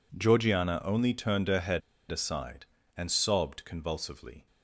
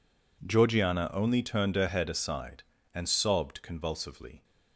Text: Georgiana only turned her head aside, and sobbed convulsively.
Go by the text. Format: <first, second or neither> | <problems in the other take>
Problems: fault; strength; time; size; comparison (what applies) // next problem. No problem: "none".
second | pauses between "head" and "aside"; slight; at 1.8 s; 0.31 s long